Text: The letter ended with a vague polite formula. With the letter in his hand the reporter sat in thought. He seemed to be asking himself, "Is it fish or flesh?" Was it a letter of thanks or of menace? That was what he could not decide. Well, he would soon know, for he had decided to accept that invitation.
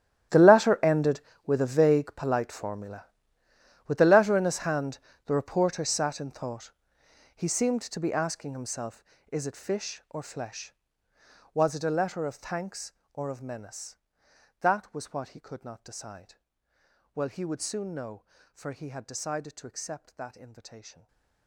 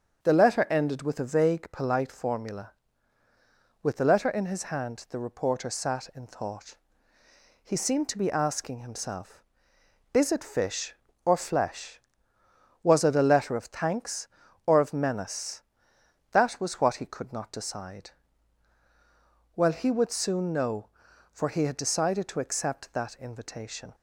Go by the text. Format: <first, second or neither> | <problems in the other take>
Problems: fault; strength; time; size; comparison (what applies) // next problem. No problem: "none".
second | gets quieter; strong; throughout; 19.5 dB // starts louder than the rest; strong; until 1.6 s; 11.5 dB; also in the second // pauses between "hand" and "the"; slight; at 4.9 s; 0.26 s long // stays silent after the last word; slight; from 20.9 s on; 0.5 s long